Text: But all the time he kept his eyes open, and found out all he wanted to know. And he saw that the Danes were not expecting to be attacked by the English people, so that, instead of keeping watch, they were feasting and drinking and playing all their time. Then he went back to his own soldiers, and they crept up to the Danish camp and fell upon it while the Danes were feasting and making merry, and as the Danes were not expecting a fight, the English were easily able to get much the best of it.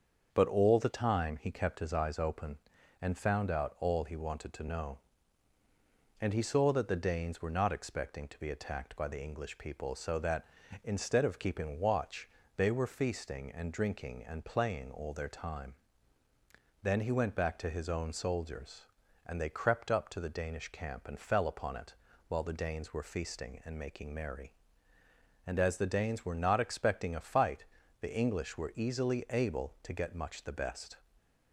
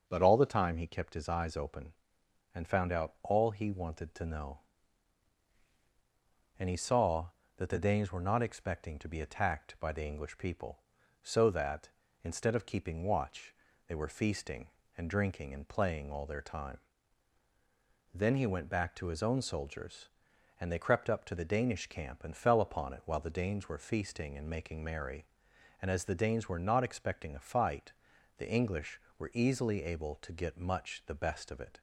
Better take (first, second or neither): second